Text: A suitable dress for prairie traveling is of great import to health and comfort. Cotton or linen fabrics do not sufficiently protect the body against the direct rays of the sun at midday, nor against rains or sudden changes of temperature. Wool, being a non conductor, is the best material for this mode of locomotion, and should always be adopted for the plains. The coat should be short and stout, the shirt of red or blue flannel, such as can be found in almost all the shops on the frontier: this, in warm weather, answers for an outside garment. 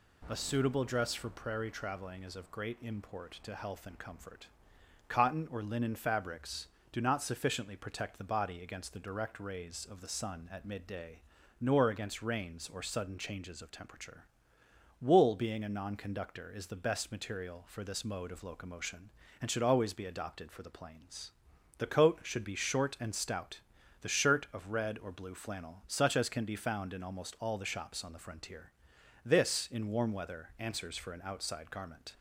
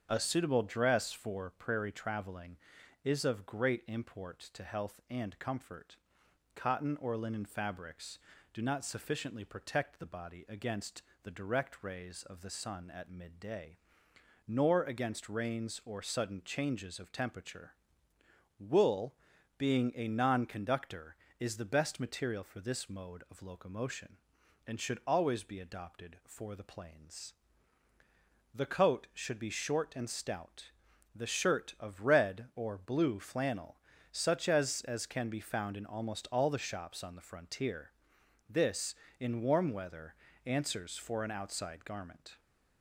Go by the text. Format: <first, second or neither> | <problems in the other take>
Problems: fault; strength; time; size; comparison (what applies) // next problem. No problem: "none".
first | starts louder than the rest; strong; until 1.1 s; 8 dB // pauses between "against" and "the"; slight; at 11.0 s; 0.18 s long // says "as" twice; at 34.8 s